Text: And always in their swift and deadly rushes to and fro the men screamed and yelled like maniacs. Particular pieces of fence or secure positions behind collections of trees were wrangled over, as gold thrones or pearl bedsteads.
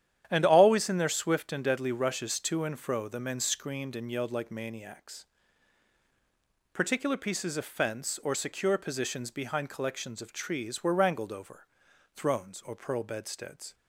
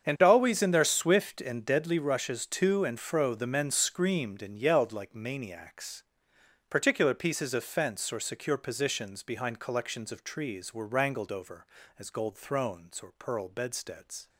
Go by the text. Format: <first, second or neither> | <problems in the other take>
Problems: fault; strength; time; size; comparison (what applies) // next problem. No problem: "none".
second | starts louder than the rest; strong; until 1.3 s; 10 dB; also in the second // skips "as gold"; at 11.9 s